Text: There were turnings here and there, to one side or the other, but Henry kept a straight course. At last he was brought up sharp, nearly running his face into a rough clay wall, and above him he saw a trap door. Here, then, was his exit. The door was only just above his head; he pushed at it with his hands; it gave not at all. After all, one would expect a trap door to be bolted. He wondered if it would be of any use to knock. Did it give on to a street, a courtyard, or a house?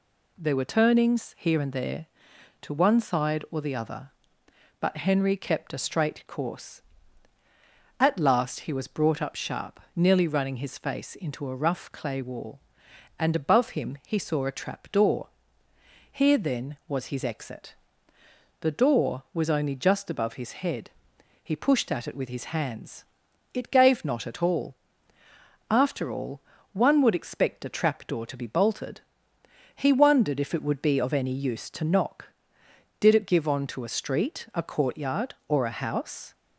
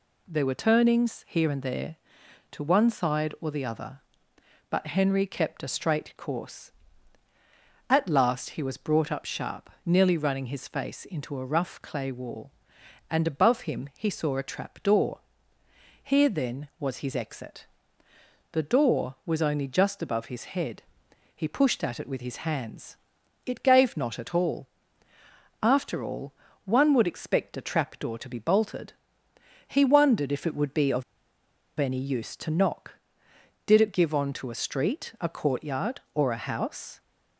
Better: first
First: none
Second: pauses between "of" and "any"; noticeable; at 31.0 s; 0.77 s long

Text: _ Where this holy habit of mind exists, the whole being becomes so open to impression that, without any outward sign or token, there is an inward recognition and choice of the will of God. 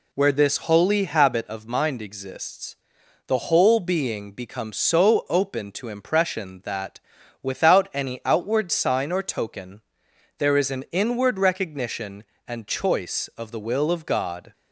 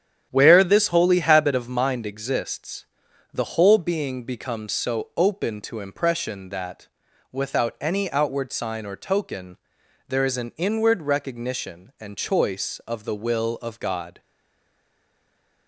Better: first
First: none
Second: starts louder than the rest; strong; until 1.3 s; 9.5 dB // stays silent after the last word; noticeable; from 14.2 s on; 1.4 s long

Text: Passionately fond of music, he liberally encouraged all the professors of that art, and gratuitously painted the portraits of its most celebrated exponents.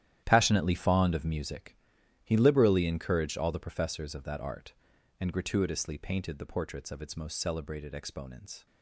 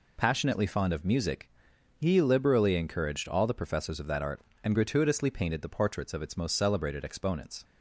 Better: second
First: gets quieter; strong; throughout; 14.5 dB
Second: none

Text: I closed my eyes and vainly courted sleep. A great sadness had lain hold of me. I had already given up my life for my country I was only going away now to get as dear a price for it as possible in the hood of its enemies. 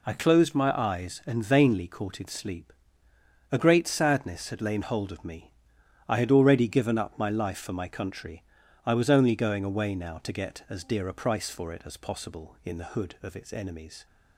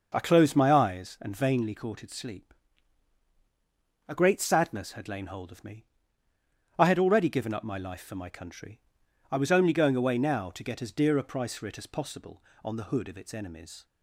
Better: first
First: pauses between "country" and "I"; at 8.4 s; 0.42 s long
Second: pauses between "country" and "I"; noticeable; at 8.7 s; 0.52 s long // says "on" for "in"; at 12.6 s

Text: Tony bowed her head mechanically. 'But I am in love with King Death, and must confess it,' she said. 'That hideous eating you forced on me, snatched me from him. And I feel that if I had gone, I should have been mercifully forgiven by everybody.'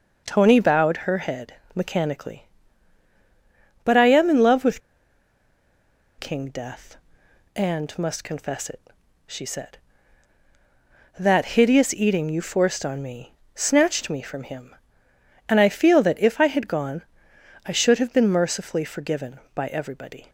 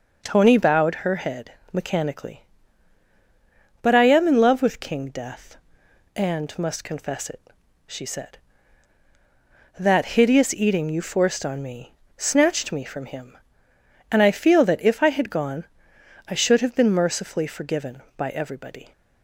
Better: second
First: pauses between "head" and "mechanically"; slight; at 1.5 s; 0.20 s long // pauses between "with" and "King"; strong; at 4.8 s; 1.3 s long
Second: pauses between "head" and "mechanically"; slight; at 1.5 s; 0.20 s long

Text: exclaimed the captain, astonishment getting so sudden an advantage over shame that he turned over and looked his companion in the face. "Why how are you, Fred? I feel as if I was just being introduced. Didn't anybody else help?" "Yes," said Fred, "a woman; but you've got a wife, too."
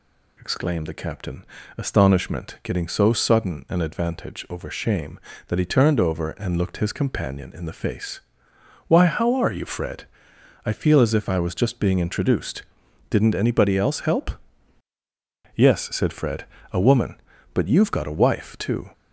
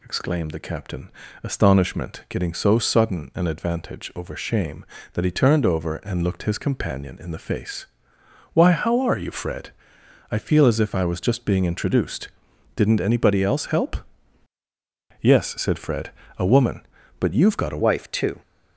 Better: first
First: none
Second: changes voice at "wife"; from 17.8 s on; 0.6 s long

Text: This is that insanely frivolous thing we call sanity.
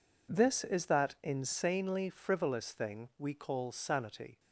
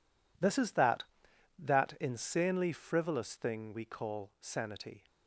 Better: first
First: none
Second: says "that" twice; at 1.5 s

